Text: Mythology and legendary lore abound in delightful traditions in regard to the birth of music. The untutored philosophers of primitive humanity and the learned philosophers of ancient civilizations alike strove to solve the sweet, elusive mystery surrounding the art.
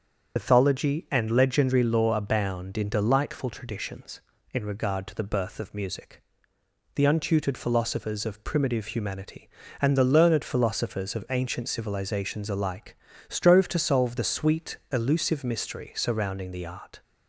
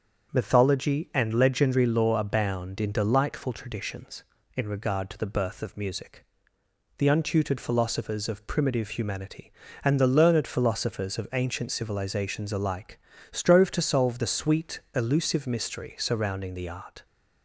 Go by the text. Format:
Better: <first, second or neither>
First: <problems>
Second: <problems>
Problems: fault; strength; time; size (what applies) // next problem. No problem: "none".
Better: second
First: loses the start of "Mythology"; at 0.3 s; 75 ms // starts louder than the rest; until 1.3 s; 7 dB // pauses between "alike" and "strove"; slight; at 12.9 s; 0.32 s long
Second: starts louder than the rest; until 1.3 s; 7 dB // pauses between "alike" and "strove"; slight; at 12.9 s; 0.32 s long